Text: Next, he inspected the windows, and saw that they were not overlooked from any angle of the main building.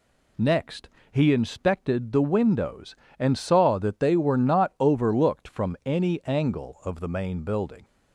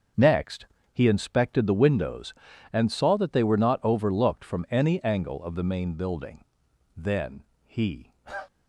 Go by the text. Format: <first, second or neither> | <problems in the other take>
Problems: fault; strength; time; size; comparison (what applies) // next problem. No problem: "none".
first | starts louder than the rest; until 1.4 s; 6.5 dB // goes on to say "Then he"; noticeable; from 6.9 s on; 1.1 s long